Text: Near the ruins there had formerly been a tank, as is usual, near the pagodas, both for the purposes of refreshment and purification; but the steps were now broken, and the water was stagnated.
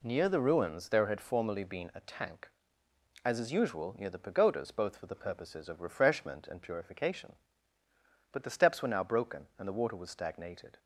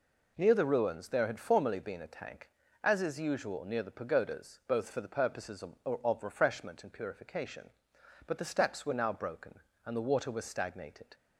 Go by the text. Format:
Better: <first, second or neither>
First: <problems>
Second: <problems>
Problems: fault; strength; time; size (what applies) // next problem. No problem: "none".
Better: first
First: none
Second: says "of" twice; at 5.8 s